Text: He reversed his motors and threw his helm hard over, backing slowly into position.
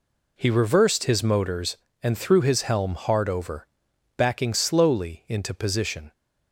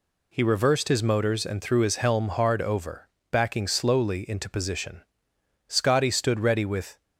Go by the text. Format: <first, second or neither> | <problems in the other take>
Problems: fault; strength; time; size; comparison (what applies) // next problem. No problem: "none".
first | goes on to say "Scotty stood ready with"; from 5.6 s on; 1.3 s long